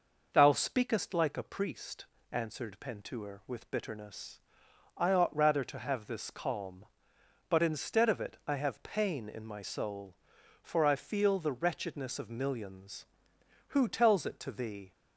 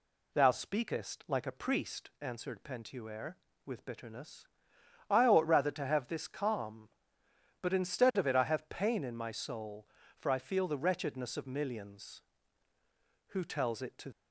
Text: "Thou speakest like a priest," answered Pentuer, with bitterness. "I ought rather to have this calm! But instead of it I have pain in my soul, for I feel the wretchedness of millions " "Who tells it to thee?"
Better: first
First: none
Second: stops before "thee"; at 14.1 s

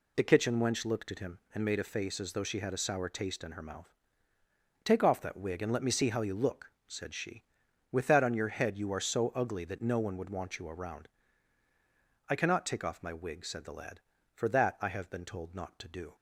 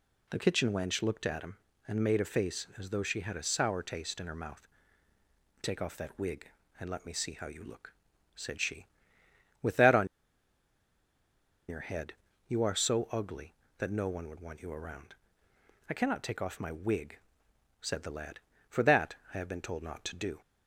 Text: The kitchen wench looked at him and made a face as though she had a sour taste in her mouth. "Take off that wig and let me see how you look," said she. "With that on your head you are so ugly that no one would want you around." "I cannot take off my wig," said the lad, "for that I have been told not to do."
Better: first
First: none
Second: pauses between "on" and "your"; strong; at 10.0 s; 1.6 s long // pauses between "head" and "you"; slight; at 12.1 s; 0.34 s long // pauses between "that" and "I"; slight; at 19.1 s; 0.18 s long

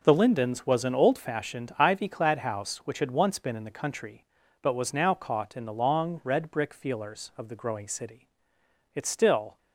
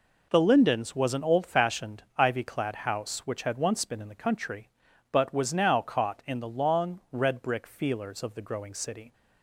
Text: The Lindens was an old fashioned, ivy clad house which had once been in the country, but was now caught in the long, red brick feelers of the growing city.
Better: second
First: goes on to say "It still"; noticeable; from 8.9 s on; 0.62 s long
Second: none

